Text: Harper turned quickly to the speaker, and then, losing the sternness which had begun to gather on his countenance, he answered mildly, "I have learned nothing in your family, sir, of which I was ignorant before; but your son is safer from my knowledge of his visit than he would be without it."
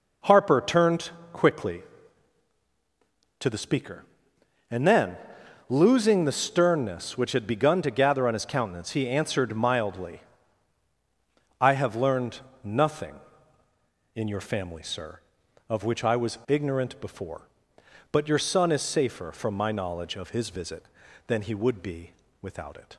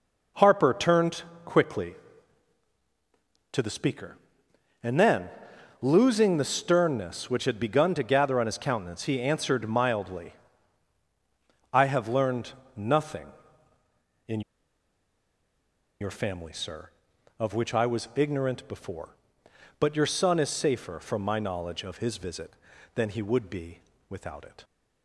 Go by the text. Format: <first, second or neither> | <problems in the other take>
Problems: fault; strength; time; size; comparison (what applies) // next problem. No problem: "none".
first | pauses between "turned" and "quickly"; slight; at 1.2 s; 0.22 s long; slight in the first // pauses between "learned" and "nothing"; slight; at 12.5 s; 0.22 s long; slight in the first // pauses between "in" and "your"; strong; at 14.4 s; 1.6 s long // pauses between "be" and "without"; slight; at 23.7 s; 0.28 s long; slight in the first